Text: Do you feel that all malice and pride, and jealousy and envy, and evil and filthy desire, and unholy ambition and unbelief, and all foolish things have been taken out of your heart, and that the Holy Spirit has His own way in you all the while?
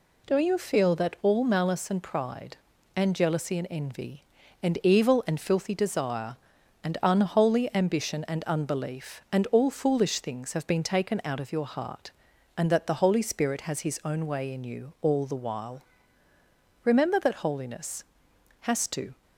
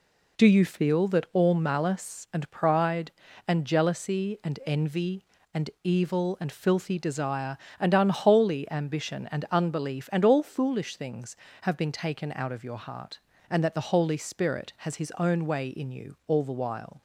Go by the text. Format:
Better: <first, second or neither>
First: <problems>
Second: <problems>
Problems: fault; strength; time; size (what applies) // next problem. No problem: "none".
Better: second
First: goes on to say "Remember that Holiness has to"; strong; from 16.8 s on; 2.3 s long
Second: none